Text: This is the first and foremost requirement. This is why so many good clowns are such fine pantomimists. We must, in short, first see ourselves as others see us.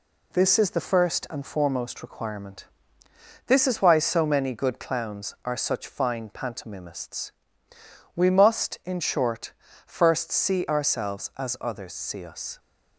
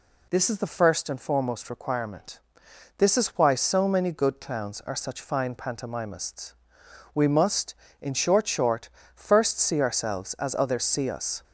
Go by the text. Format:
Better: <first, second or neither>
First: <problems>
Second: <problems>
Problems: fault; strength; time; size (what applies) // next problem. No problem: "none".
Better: first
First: none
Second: says "short" twice; at 8.4 s